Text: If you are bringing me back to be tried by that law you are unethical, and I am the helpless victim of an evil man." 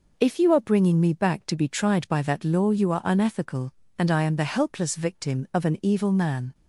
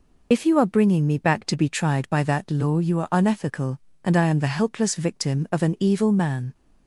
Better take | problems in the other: first | loses the start of "If"; at 0.3 s; 50 ms

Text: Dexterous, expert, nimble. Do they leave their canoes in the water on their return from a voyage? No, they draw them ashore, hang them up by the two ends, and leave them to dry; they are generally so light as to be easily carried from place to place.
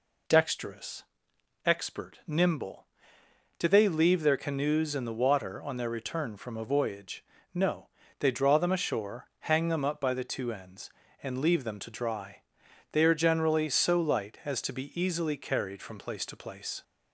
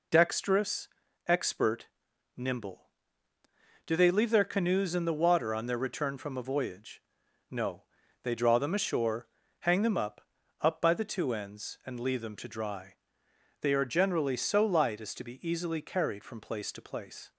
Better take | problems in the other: first | says "up" twice; at 10.6 s

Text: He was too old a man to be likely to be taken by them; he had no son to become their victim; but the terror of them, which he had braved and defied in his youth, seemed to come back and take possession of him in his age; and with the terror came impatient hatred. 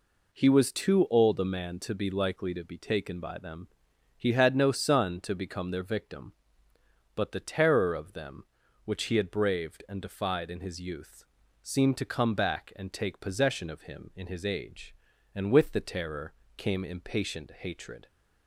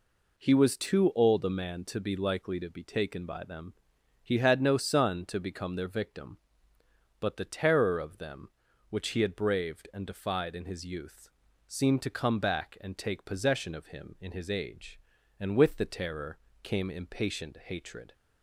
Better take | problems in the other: neither | pauses between "terror" and "came"; slight; the same in both

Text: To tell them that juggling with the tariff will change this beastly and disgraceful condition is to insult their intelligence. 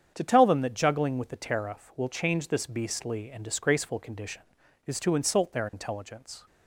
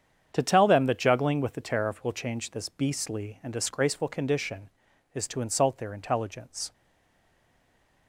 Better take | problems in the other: first | starts louder than the rest; strong; until 1.3 s; 8 dB; strong in the first // stays silent after the last word; noticeable; from 6.7 s on; 1.3 s long

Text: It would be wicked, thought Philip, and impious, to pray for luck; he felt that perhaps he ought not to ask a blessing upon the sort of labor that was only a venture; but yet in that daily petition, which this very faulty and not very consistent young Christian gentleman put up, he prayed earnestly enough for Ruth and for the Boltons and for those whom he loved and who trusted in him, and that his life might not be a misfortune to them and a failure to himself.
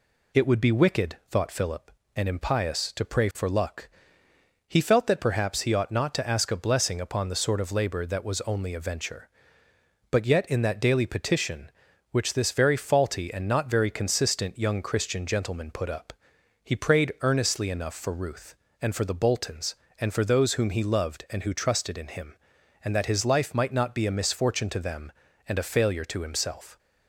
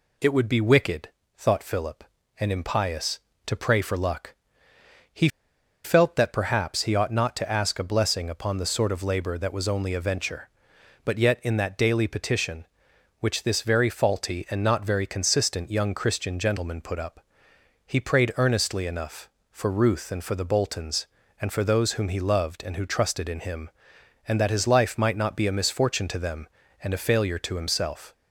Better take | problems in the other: first | pauses between "he" and "felt"; noticeable; at 5.2 s; 0.56 s long

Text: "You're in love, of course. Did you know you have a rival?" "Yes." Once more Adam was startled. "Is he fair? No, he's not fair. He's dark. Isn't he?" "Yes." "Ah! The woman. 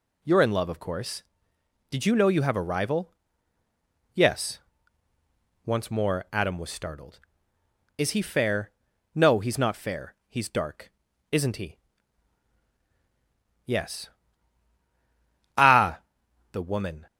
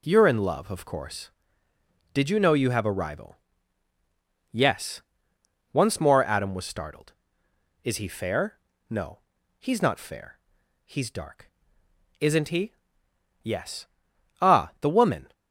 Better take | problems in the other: neither | none

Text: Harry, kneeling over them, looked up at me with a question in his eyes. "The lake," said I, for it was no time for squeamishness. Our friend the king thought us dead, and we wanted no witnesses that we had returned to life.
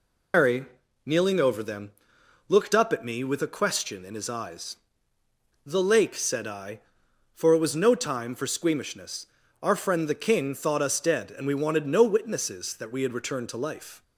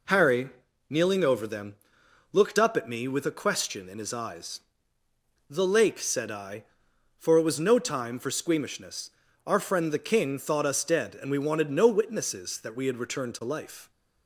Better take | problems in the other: second | loses the start of "Harry"; at 0.3 s; 120 ms

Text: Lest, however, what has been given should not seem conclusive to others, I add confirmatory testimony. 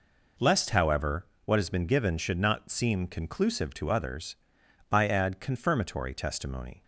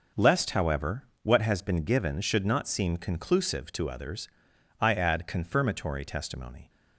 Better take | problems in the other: neither | none

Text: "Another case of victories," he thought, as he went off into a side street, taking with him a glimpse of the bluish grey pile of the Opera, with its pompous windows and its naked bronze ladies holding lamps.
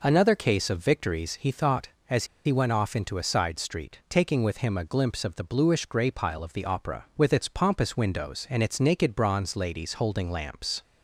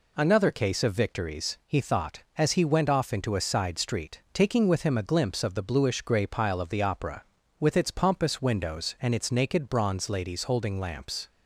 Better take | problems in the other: second | pauses between "as" and "he"; slight; at 2.2 s; 0.21 s long

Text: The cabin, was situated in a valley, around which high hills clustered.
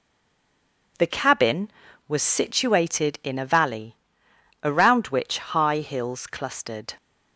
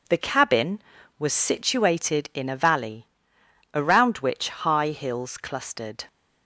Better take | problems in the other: second | stays silent before the first word; slight; until 0.9 s; 0.9 s long

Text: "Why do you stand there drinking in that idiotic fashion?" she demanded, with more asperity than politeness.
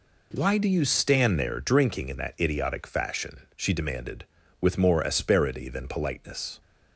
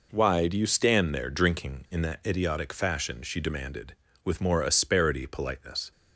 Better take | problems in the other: first | skips "than"; at 5.2 s

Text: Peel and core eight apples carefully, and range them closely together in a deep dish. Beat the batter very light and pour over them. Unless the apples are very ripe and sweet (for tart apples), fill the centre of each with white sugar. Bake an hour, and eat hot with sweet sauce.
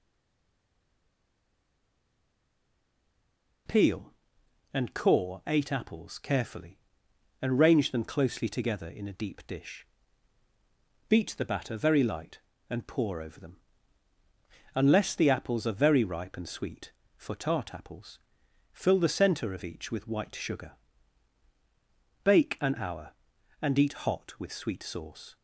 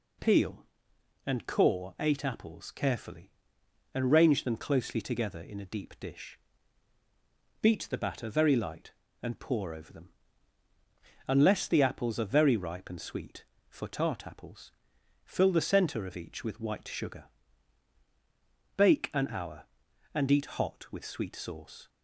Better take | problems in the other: second | stays silent before the first word; strong; until 3.6 s; 3.6 s long

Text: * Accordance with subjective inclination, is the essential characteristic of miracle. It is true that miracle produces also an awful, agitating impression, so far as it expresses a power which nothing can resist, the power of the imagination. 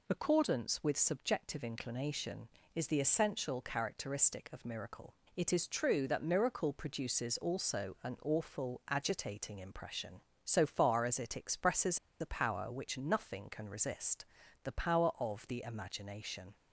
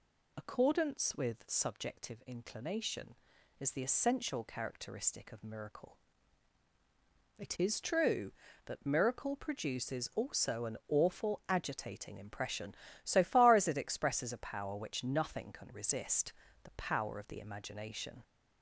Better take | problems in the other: second | pauses between "expresses" and "a"; slight; at 11.9 s; 0.22 s long

